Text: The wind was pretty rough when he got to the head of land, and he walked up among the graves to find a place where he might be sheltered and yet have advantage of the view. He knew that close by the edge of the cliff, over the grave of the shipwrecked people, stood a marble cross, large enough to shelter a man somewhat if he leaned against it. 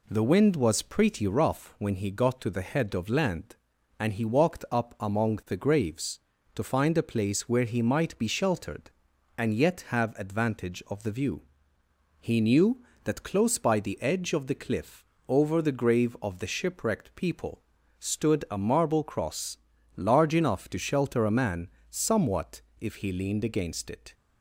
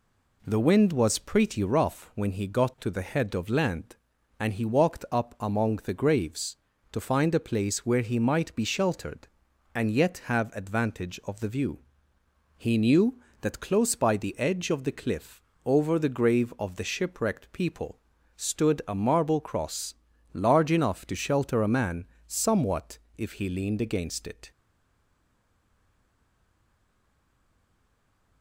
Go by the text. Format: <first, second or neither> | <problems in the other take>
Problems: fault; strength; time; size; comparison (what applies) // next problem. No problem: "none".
first | pauses between "man" and "somewhat"; slight; at 22.0 s; 0.22 s long; slight in the first // pauses between "somewhat" and "if"; slight; at 22.9 s; 0.18 s long; slight in the first // stays silent after the last word; strong; from 24.5 s on; 3.9 s long